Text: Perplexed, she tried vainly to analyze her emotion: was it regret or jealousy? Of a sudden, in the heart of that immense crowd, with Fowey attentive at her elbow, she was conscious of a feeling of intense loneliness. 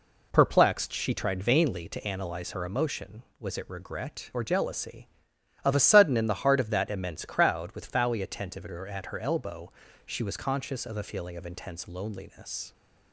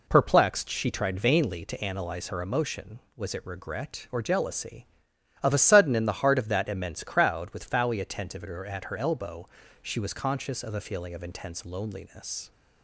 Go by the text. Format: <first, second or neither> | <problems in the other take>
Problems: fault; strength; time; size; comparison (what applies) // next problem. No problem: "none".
neither | none